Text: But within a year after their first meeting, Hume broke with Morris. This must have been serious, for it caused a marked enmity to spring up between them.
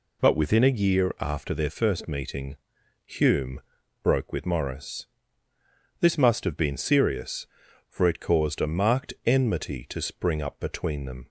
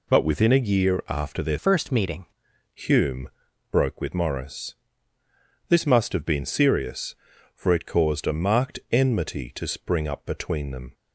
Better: first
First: pauses between "Hume" and "broke"; at 3.6 s; 0.42 s long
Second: changes voice from "first" to "meeting"; from 1.5 to 2.2 s; 0.7 s long // pauses between "Hume" and "broke"; at 3.2 s; 0.42 s long

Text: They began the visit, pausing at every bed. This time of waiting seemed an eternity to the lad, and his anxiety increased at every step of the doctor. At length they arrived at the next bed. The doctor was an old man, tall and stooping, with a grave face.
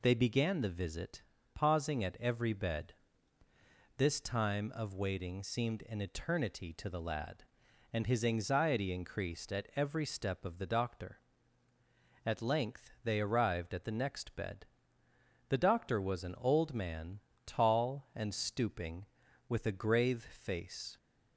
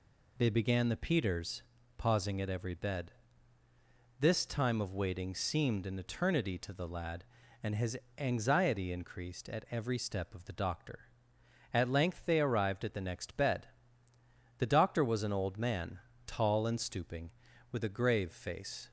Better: first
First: none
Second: says "peters" for "visit"; at 0.9 s // pauses between "his" and "anxiety"; slight; at 7.9 s; 0.22 s long

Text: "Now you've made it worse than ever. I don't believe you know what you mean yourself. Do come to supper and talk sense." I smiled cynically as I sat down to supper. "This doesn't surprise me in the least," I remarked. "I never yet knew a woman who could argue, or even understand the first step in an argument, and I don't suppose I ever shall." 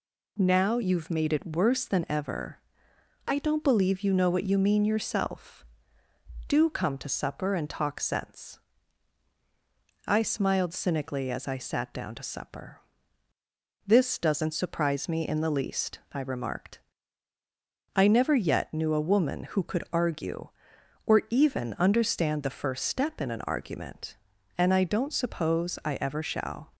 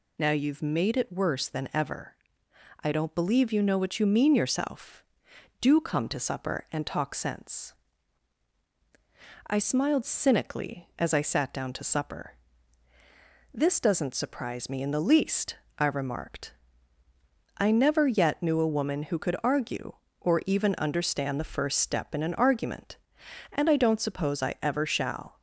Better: neither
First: none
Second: none

